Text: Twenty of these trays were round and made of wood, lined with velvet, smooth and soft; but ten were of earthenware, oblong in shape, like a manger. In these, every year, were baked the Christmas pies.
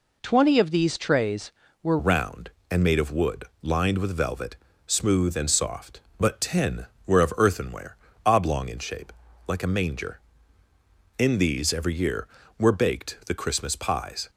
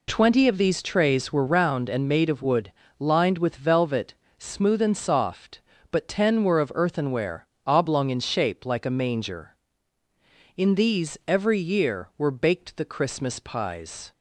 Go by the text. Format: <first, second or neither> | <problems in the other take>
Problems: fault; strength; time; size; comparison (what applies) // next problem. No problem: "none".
second | changes voice at "round"; from 1.9 s on; 12.3 s long